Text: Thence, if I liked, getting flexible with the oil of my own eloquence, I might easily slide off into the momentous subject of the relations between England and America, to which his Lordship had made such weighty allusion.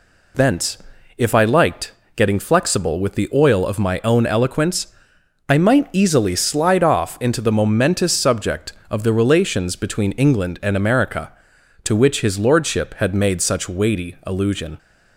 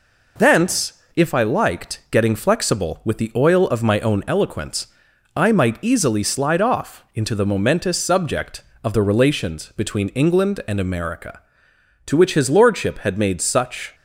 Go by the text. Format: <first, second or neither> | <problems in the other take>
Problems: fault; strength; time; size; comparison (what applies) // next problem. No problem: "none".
first | stops before "weighty allusion"; at 13.9 s